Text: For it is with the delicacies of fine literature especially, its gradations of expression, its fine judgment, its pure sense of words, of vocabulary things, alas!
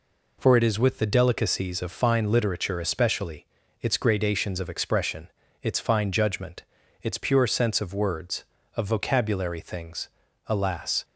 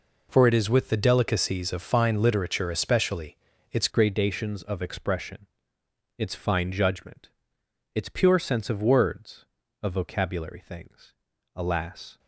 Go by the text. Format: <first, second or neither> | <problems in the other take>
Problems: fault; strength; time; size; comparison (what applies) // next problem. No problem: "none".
first | changes voice at "gradations"; from 3.8 s on; 8.3 s long